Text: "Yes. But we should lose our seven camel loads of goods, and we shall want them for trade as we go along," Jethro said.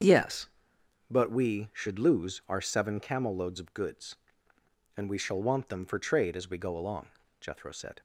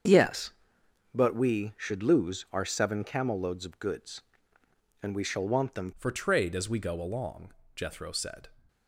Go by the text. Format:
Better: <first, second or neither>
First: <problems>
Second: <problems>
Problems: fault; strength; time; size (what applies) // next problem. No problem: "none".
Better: first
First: starts louder than the rest; strong; until 1.6 s; 7.5 dB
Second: starts louder than the rest; until 1.6 s; 7 dB // changes voice at "for"; from 5.9 s on; 2.5 s long